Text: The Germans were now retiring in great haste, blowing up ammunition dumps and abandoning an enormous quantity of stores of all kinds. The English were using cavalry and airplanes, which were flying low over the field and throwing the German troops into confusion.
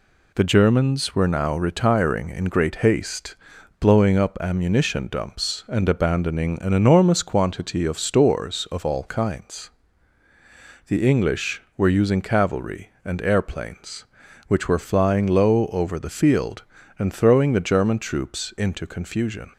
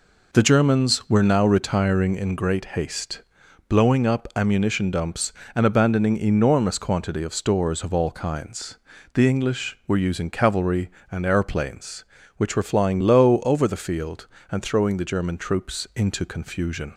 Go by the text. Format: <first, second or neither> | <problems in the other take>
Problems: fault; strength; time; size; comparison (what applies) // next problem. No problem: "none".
first | skips "an"; at 6.1 s